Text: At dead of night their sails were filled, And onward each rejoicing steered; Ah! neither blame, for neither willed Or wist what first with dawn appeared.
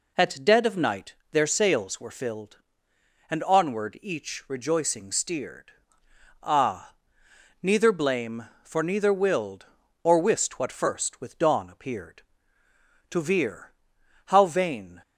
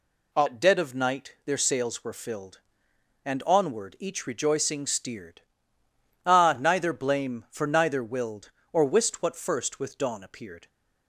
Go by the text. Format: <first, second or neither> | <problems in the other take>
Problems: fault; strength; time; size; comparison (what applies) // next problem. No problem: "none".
second | pauses between "night" and "their"; slight; at 1.1 s; 0.18 s long // goes on to say "To veer how vain"; strong; from 13.0 s on; 1.9 s long